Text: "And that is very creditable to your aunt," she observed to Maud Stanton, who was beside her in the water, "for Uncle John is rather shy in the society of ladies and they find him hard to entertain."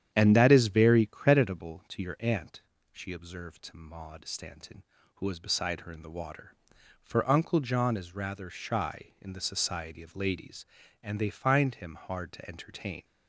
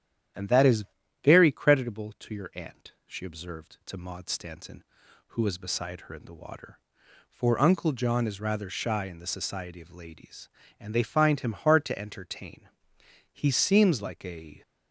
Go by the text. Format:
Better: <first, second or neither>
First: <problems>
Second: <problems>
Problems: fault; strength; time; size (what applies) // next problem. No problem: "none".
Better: first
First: starts louder than the rest; strong; until 1.1 s; 9.5 dB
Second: starts louder than the rest; strong; until 1.7 s; 11 dB // pauses between "is" and "very"; at 0.8 s; 0.40 s long // goes on to say "He seems like a"; noticeable; from 13.3 s on; 1.2 s long